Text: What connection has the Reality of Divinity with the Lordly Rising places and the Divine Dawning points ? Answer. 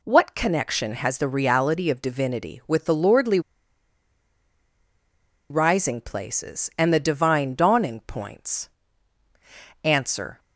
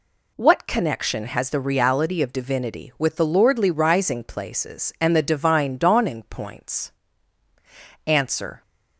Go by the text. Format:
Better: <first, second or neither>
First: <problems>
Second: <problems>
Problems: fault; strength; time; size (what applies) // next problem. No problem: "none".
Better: second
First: pauses between "Lordly" and "Rising"; strong; at 3.3 s; 2.1 s long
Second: none